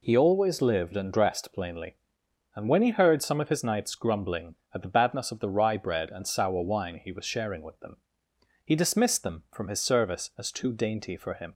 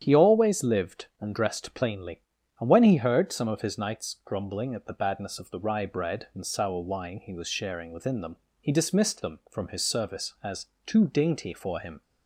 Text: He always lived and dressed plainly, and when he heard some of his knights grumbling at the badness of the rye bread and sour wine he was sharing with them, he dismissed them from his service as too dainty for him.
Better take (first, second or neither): first